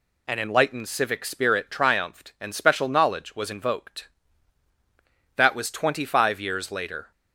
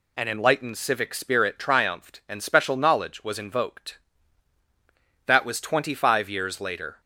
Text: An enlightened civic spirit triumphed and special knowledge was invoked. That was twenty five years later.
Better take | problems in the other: neither | none

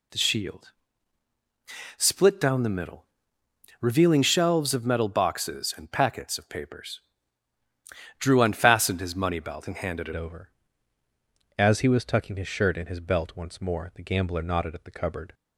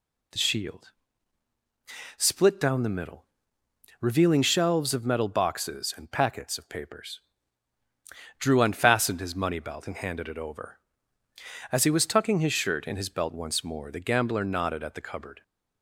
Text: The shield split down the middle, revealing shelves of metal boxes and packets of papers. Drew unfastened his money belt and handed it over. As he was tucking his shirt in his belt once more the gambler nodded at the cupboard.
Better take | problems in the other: second | pauses between "shield" and "split"; strong; at 0.7 s; 1.2 s long; strong in the second // changes voice at "over"; from 10.1 s on; 5.2 s long

